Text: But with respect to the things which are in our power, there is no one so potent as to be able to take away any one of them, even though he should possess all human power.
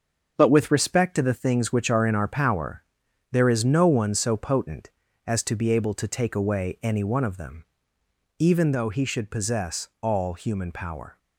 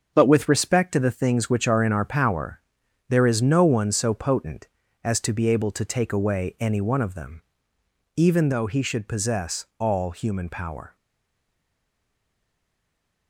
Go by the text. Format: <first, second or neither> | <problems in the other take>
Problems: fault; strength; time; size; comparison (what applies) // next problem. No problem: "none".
first | starts louder than the rest; until 1.1 s; 7 dB; also in the first // stays silent after the last word; from 10.9 s on; 2.3 s long